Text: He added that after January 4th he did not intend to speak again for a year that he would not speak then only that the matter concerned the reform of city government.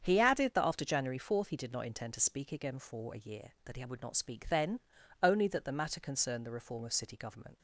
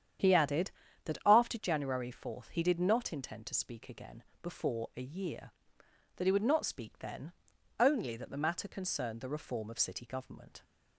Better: first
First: starts louder than the rest; strong; until 1.0 s; 7.5 dB // pauses between "then" and "only"; at 4.7 s; 0.42 s long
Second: starts louder than the rest; strong; until 1.6 s; 9 dB // says "before" for "for"; at 4.4 s // pauses between "then" and "only"; at 7.3 s; 0.44 s long

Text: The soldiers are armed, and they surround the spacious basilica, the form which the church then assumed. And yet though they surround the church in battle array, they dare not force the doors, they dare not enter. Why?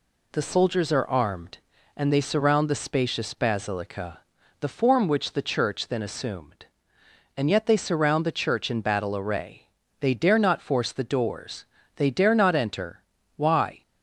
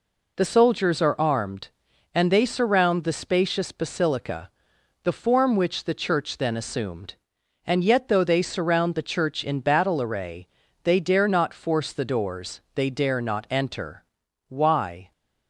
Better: second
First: skips "though"; at 7.6 s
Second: none

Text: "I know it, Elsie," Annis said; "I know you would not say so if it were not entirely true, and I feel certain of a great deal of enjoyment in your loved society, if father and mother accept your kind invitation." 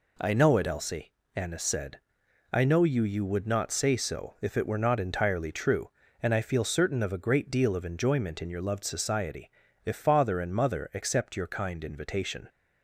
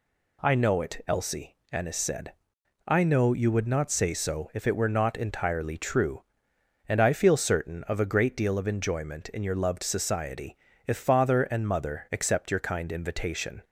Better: second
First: says "you" twice; at 3.0 s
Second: none

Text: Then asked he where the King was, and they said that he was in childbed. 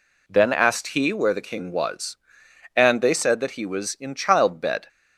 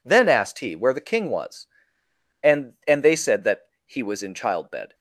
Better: first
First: none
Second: says "and" twice; at 2.8 s // pauses between "that" and "he"; slight; at 3.6 s; 0.18 s long

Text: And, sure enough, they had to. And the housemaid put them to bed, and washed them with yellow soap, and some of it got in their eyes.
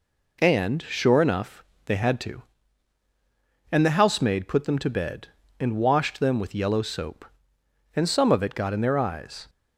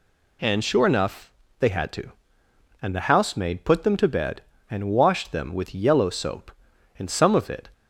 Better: first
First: none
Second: stops before "got in their eyes"; at 7.7 s

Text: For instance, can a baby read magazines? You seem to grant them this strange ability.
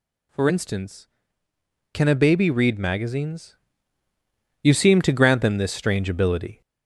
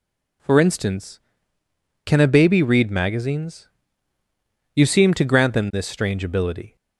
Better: second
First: gets louder; noticeable; throughout; 4 dB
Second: none

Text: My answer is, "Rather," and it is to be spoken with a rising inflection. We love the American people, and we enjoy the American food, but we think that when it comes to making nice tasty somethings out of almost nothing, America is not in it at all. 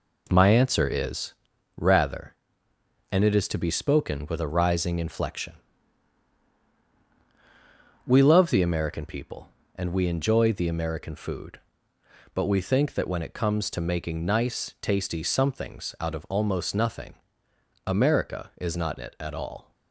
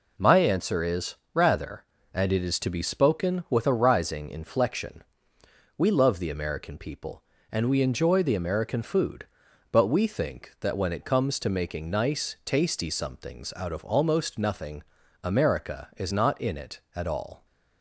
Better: second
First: skips "in"; at 18.9 s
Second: none

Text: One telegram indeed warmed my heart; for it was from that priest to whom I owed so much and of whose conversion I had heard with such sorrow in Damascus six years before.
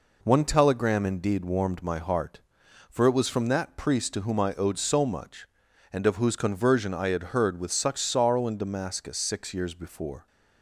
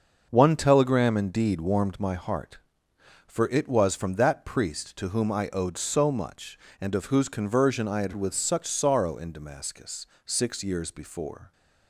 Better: first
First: none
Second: starts louder than the rest; noticeable; until 1.3 s; 6 dB // skips "heard"; at 8.1 s // pauses between "Damascus" and "six"; slight; at 10.0 s; 0.18 s long

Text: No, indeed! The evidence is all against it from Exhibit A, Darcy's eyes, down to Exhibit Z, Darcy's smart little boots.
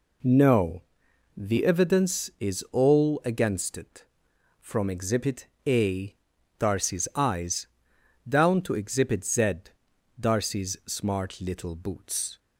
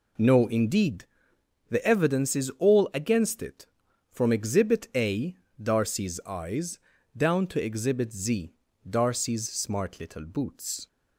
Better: second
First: skips "indeed"; at 1.0 s // pauses between "Exhibit" and "A"; slight; at 5.4 s; 0.18 s long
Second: none

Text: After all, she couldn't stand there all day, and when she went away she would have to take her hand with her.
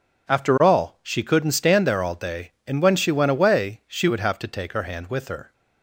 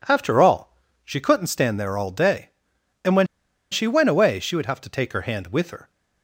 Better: first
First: none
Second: pauses between "when" and "she"; at 3.2 s; 0.45 s long

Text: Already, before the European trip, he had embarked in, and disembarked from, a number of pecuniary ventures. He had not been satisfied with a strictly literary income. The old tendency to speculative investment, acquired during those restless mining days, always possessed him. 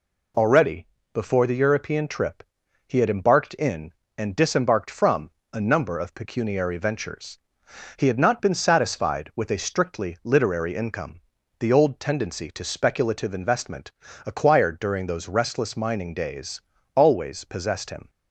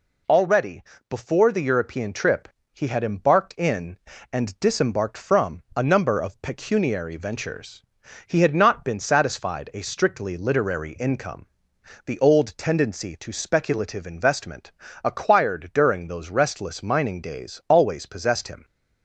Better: first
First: none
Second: skips "with"; at 9.7 s

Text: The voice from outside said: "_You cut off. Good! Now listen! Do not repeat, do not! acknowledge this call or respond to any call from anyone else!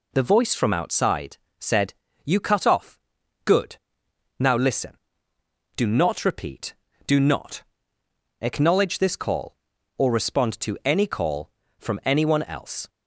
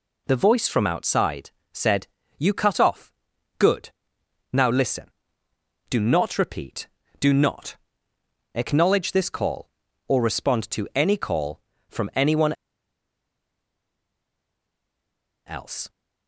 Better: first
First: pauses between "outside" and "said"; slight; at 1.3 s; 0.22 s long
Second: pauses between "outside" and "said"; slight; at 1.5 s; 0.22 s long // pauses between "anyone" and "else"; strong; at 12.5 s; 2.9 s long

